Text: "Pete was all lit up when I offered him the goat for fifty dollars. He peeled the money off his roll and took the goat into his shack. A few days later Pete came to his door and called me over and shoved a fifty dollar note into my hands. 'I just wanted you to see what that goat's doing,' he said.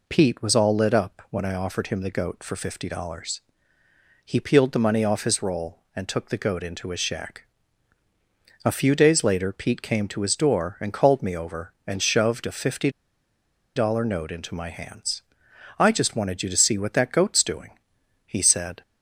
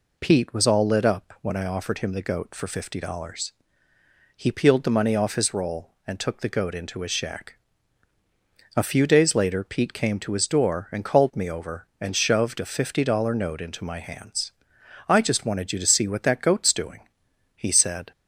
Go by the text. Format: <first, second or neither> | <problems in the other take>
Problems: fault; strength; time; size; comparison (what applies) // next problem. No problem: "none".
second | pauses between "fifty" and "dollar"; noticeable; at 12.8 s; 0.86 s long